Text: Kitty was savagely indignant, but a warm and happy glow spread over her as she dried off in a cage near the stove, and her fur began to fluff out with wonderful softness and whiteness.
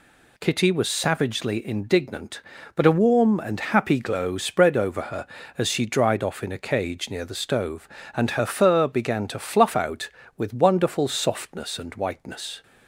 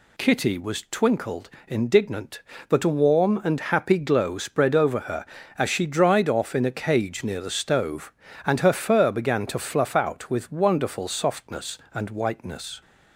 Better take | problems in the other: first | says "twinkled" for "savagely"; at 0.9 s

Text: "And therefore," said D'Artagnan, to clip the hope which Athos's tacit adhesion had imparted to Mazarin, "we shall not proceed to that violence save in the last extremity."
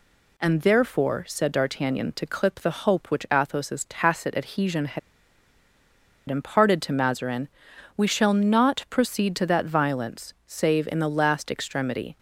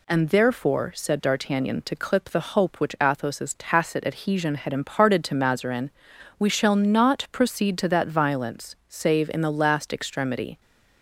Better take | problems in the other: second | pauses between "had" and "imparted"; strong; at 4.9 s; 1.3 s long

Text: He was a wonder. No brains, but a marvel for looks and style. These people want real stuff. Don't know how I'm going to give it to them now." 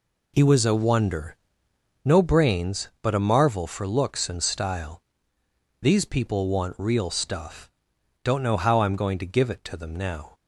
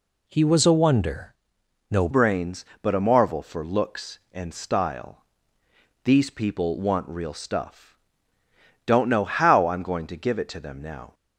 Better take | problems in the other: first | changes voice at "brains"; from 2.1 s on; 9.0 s long

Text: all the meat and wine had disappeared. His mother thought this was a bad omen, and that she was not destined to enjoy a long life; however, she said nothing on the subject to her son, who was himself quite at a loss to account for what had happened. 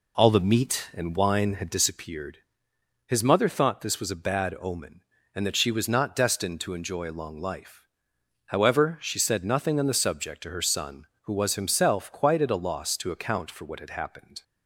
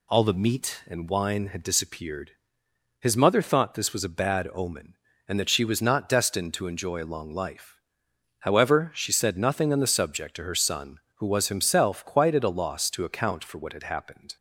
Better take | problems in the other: second | starts louder than the rest; slight; until 2.0 s; 3 dB

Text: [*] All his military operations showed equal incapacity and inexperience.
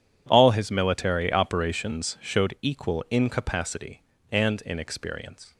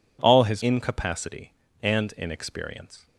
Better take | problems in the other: first | skips "military operations showed equal"; at 0.6 s

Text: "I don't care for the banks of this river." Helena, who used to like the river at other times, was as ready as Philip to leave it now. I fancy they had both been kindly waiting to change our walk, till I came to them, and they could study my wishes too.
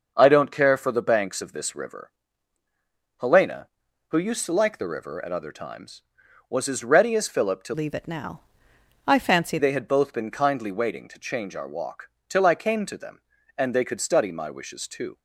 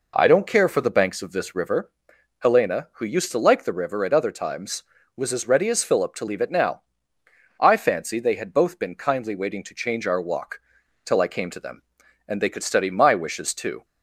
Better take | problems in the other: second | starts louder than the rest; until 1.1 s; 6 dB // changes voice from "leave" to "fancy"; from 7.7 to 9.5 s; 1.8 s long

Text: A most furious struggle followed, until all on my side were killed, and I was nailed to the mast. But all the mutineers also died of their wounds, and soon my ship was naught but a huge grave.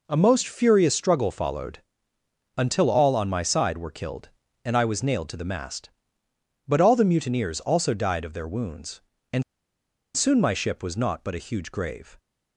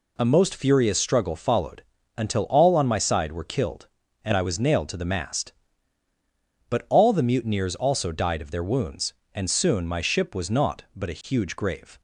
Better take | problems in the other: second | pauses between "and" and "soon"; noticeable; at 9.4 s; 0.71 s long

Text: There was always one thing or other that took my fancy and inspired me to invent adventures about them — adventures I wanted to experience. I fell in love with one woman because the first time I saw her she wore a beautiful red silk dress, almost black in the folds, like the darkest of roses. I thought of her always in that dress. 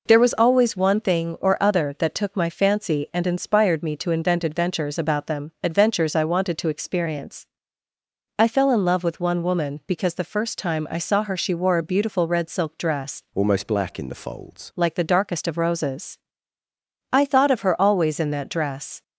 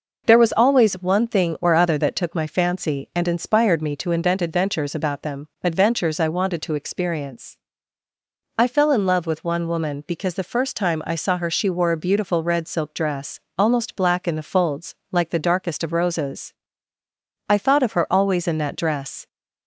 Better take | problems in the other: second | changes voice from "almost" to "folds"; from 13.3 to 14.7 s; 1.4 s long

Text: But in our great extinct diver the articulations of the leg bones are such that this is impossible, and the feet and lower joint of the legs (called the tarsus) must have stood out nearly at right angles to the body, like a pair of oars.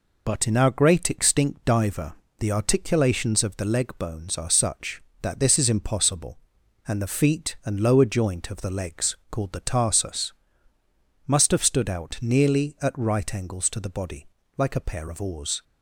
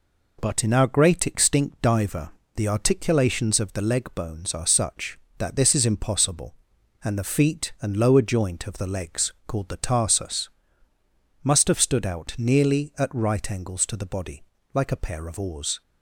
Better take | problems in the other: second | loses the start of "But"; at 0.2 s; 40 ms // pauses between "diver" and "the"; slight; at 2.1 s; 0.26 s long; slight in the second

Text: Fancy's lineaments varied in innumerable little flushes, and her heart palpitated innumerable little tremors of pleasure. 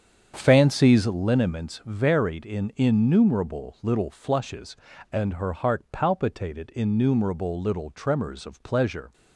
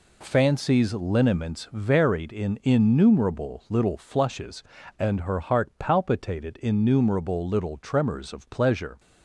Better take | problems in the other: second | starts louder than the rest; strong; until 1.2 s; 7.5 dB

